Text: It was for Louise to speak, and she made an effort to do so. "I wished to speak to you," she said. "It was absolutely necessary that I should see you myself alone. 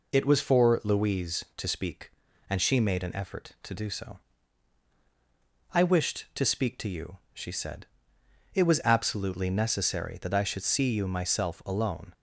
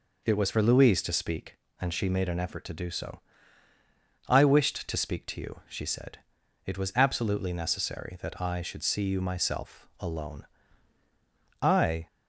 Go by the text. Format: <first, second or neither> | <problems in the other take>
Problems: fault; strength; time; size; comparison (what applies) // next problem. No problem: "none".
first | goes on to say "I"; slight; from 11.6 s on; 0.46 s long